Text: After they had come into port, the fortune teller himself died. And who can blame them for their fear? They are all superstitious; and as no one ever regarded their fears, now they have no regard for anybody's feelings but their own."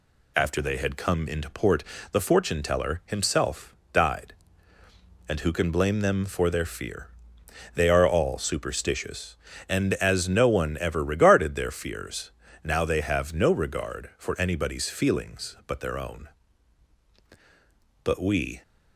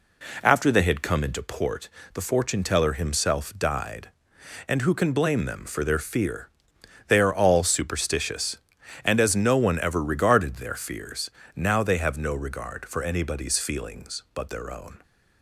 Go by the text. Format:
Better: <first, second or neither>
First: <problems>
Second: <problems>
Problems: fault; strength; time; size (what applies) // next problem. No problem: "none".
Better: second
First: pauses between "himself" and "died"; slight; at 3.7 s; 0.18 s long // goes on to say "But we"; from 18.0 s on; 0.58 s long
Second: none